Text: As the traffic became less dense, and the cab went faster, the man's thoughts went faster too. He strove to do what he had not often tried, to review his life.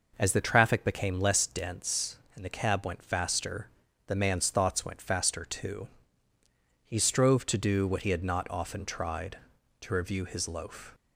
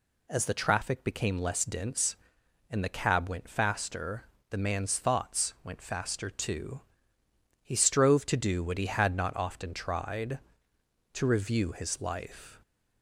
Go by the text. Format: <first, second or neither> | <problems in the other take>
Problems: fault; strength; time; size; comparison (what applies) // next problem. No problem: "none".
second | says "loaf" for "life"; at 10.4 s